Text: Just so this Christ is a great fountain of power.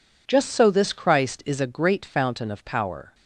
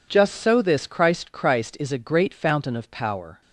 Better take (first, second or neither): first